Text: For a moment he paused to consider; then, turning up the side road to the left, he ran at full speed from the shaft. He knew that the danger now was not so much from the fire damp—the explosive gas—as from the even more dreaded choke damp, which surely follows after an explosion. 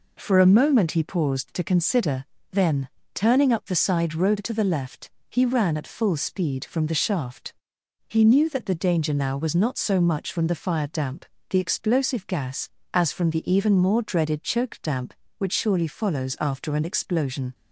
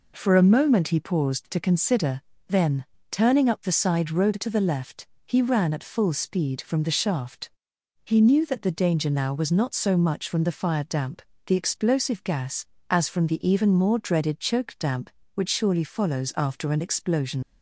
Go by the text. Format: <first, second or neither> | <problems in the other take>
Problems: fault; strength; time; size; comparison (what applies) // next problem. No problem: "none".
first | leaves "explosion" unfinished; at 17.4 s; 80 ms